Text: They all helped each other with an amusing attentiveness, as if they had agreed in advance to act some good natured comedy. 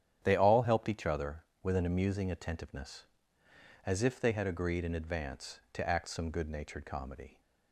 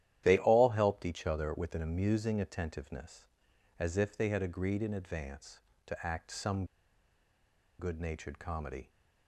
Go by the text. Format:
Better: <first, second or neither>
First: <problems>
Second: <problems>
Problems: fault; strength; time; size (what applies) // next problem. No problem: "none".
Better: first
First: starts louder than the rest; strong; until 1.2 s; 9.5 dB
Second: starts louder than the rest; strong; until 1.2 s; 11.5 dB // pauses between "some" and "good"; at 6.6 s; 1.1 s long